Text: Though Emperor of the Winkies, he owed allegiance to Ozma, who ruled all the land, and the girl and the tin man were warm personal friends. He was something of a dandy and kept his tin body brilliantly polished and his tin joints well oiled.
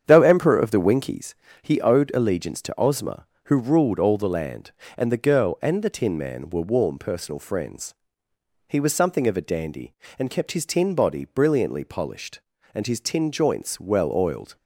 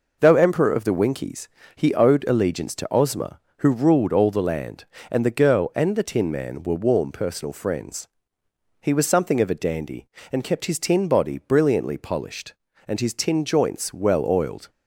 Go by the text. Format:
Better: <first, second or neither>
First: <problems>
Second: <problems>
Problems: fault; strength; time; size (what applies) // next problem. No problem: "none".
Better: second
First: starts louder than the rest; strong; until 1.2 s; 8.5 dB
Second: none